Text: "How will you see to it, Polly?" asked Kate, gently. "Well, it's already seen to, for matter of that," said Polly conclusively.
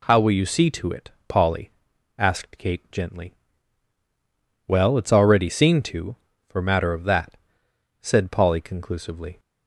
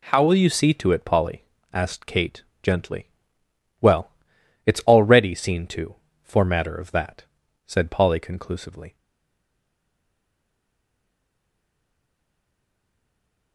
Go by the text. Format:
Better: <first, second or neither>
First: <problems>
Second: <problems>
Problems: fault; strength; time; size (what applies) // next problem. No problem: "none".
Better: first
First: none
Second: stays silent after the last word; strong; from 8.9 s on; 4.6 s long